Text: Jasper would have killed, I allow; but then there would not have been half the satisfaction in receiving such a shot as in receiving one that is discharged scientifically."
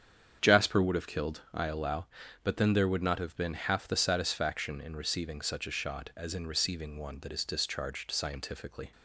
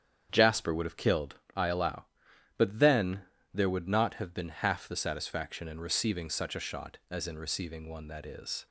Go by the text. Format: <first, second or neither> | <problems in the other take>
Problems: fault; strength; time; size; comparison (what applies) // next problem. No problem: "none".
first | starts louder than the rest; strong; until 1.3 s; 8.5 dB; strong in the first // pauses between "then" and "there"; slight; at 3.2 s; 0.30 s long // stops before "discharged scientifically"; at 8.6 s